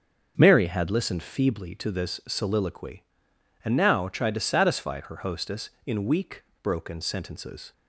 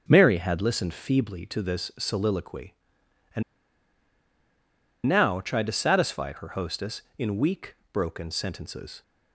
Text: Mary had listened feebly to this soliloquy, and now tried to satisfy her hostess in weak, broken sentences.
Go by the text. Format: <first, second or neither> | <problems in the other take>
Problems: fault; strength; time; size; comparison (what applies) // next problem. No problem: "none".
first | starts louder than the rest; until 1.0 s; 6.5 dB; also in the first // pauses between "and" and "now"; strong; at 3.4 s; 1.6 s long